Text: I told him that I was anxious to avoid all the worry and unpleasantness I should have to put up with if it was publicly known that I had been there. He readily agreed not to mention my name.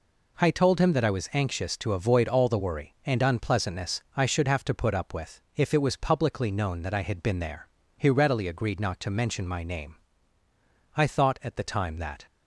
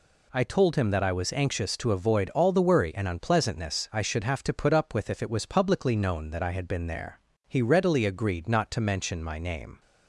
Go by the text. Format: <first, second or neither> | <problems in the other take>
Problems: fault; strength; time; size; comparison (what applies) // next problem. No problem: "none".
second | pauses between "unpleasantness" and "I"; slight; at 4.0 s; 0.16 s long // goes on to say "I thought at the time that"; noticeable; from 10.9 s on; 1.3 s long